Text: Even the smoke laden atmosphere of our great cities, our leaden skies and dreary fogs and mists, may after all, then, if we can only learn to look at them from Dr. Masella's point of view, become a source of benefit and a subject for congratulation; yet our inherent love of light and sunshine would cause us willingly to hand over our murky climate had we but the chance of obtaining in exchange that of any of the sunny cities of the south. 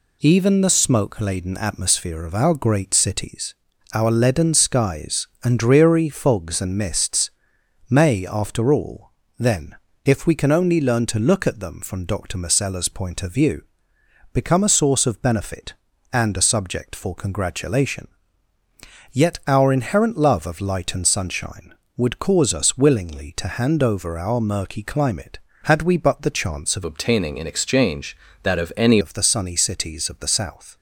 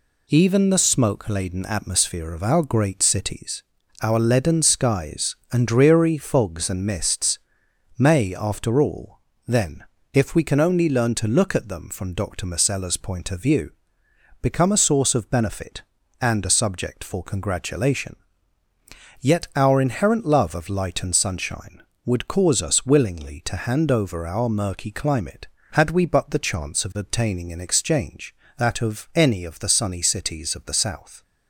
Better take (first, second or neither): second